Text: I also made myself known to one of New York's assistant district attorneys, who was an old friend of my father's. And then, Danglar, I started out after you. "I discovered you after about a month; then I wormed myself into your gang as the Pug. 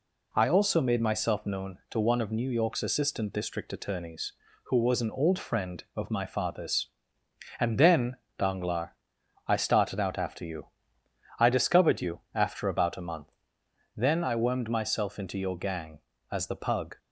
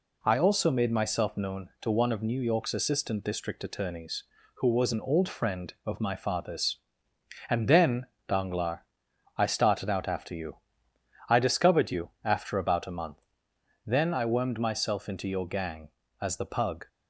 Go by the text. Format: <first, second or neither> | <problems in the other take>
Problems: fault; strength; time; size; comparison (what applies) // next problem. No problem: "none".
neither | none